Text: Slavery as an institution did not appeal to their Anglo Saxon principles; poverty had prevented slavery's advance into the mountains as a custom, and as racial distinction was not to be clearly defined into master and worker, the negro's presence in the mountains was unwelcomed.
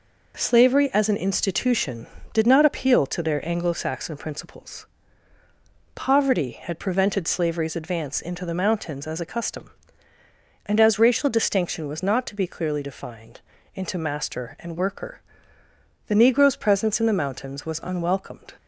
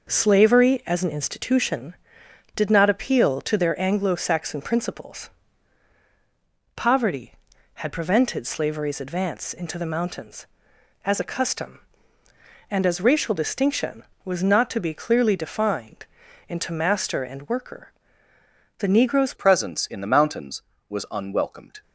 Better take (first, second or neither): first